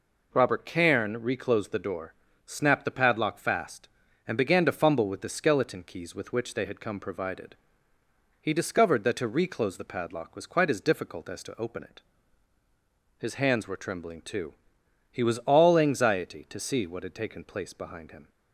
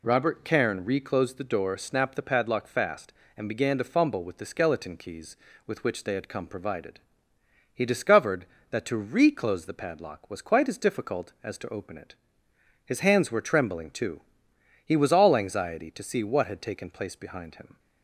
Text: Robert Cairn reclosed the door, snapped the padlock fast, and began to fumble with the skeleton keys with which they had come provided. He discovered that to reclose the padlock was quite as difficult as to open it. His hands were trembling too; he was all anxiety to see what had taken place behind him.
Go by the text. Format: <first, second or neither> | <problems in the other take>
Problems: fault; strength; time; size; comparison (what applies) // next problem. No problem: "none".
neither | none